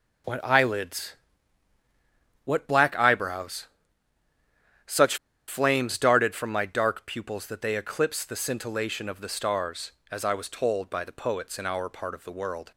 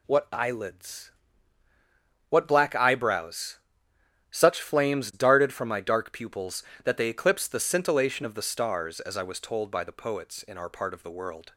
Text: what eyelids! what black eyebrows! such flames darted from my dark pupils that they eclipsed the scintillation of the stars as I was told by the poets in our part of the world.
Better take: second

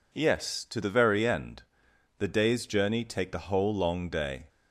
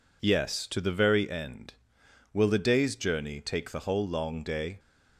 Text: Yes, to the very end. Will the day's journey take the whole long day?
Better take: second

